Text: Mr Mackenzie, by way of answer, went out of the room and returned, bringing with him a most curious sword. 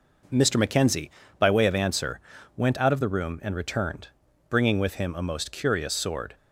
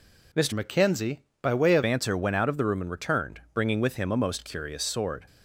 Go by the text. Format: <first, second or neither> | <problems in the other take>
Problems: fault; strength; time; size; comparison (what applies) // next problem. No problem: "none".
first | changes voice from "Mackenzie" to "of"; from 0.5 to 1.8 s; 1.3 s long